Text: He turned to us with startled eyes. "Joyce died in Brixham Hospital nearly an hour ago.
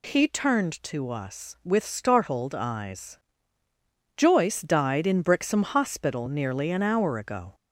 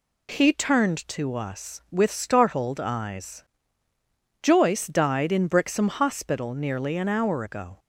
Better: second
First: gets louder; slight; throughout; 2.5 dB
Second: none

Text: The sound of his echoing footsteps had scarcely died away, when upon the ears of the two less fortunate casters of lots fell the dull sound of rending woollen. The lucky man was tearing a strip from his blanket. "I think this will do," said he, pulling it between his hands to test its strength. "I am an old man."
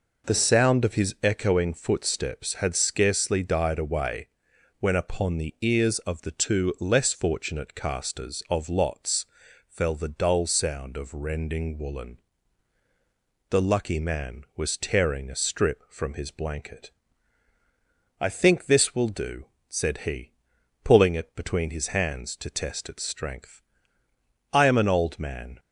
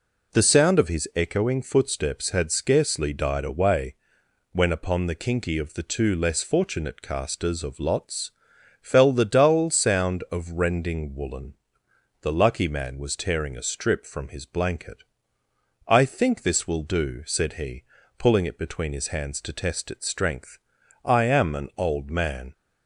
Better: first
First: pauses between "lots" and "fell"; at 9.2 s; 0.42 s long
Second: says "kinky" for "ears"; at 5.1 s // pauses between "lots" and "fell"; noticeable; at 8.3 s; 0.50 s long

